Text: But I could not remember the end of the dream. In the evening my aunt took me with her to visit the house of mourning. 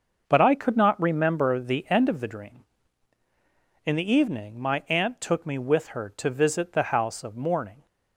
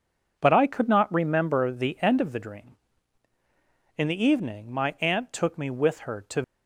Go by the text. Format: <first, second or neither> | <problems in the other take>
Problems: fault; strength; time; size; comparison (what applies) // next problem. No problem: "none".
first | stops before "visit the house of mourning"; at 6.4 s